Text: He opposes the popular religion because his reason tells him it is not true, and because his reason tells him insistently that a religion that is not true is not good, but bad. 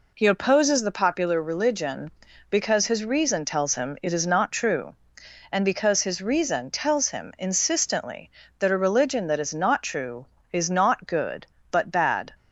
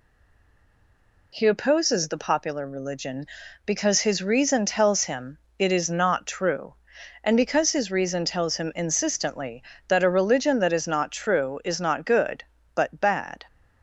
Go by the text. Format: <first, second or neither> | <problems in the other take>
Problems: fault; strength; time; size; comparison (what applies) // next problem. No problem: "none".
first | stays silent before the first word; noticeable; until 1.3 s; 1.3 s long // pauses between "him" and "it"; slight; at 5.3 s; 0.18 s long